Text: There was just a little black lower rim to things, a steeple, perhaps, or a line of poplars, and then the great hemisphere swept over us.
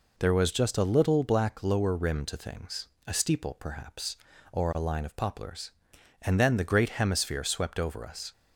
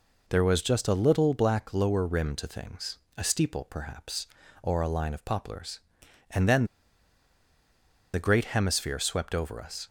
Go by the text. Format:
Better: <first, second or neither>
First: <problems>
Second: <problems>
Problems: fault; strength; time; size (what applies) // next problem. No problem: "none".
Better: first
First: none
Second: pauses between "then" and "the"; strong; at 6.6 s; 1.4 s long